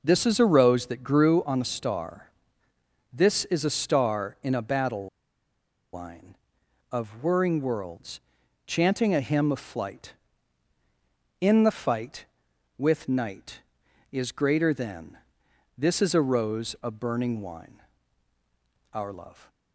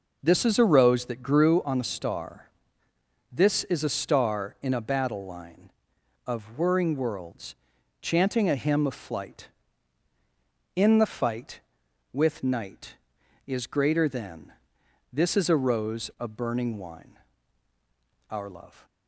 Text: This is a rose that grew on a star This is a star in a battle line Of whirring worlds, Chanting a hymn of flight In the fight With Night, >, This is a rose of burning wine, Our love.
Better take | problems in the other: second | pauses between "star" and "This"; noticeable; at 2.3 s; 0.82 s long; noticeable in the second // pauses between "battle" and "line"; noticeable; at 5.0 s; 0.86 s long

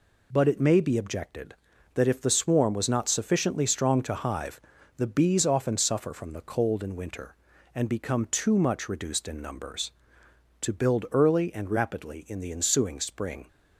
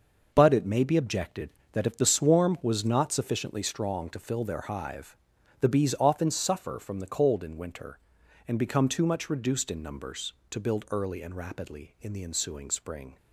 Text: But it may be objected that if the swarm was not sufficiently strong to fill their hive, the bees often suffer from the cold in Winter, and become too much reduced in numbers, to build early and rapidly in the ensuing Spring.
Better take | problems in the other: second | skips "fill their"; at 4.1 s

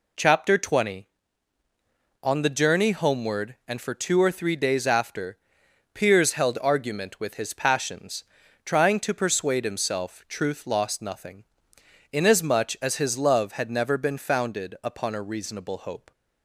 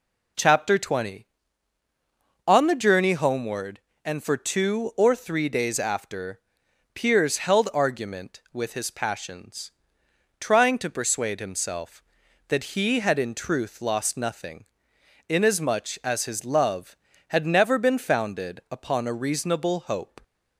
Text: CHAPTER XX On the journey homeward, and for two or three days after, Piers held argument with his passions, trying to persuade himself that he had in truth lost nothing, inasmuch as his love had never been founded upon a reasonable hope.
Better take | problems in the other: second | skips "that he had in"; at 10.2 s

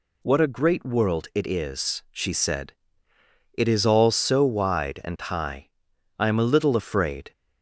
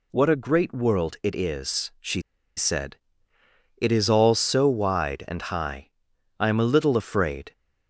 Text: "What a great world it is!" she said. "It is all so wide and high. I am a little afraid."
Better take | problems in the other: first | pauses between "she" and "said"; slight; at 2.2 s; 0.35 s long

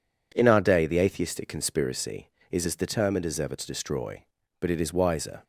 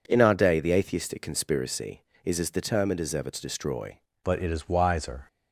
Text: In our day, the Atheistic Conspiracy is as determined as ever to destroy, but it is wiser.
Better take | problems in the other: first | changes voice at "but"; from 4.2 s on; 1.0 s long

